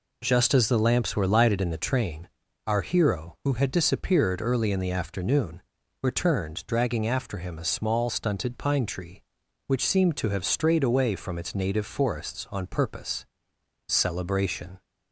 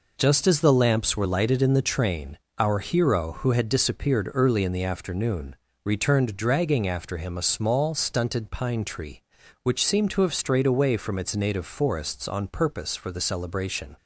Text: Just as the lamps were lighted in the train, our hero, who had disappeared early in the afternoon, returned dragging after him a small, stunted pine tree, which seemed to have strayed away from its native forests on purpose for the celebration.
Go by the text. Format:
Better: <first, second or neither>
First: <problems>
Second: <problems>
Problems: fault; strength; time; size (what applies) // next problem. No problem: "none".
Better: second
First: skips "for the"; at 13.5 s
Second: none